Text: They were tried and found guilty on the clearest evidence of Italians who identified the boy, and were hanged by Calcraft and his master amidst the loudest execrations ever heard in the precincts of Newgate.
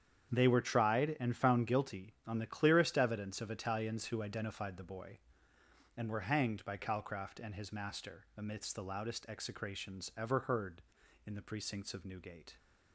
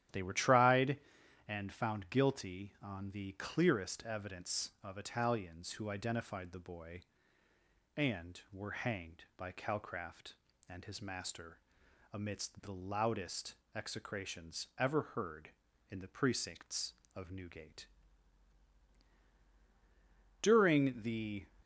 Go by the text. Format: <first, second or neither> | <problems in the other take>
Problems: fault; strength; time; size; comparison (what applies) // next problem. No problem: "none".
first | starts louder than the rest; strong; until 1.6 s; 11.5 dB; strong in the first // pauses between "master" and "amidst"; noticeable; at 11.5 s; 0.54 s long // pauses between "loudest" and "execrations"; slight; at 13.5 s; 0.20 s long // goes on to say "During the"; noticeable; from 20.4 s on; 1.0 s long